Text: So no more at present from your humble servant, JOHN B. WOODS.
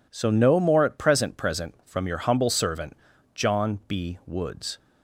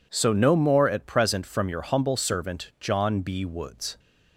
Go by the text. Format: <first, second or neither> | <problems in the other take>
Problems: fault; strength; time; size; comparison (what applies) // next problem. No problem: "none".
second | says "present" twice; at 1.3 s